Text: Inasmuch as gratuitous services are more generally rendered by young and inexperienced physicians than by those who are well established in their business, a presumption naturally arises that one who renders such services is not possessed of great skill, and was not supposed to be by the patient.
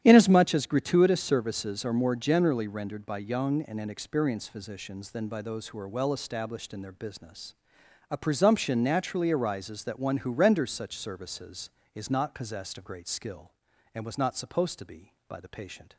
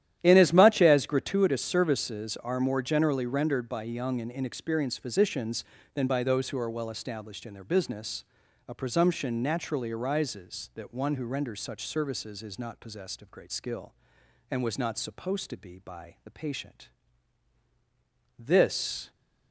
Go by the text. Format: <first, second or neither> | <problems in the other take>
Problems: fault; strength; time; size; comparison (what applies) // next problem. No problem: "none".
first | starts louder than the rest; strong; until 1.2 s; 11.5 dB; strong in the first // goes on to say "This"; noticeable; from 18.3 s on; 0.72 s long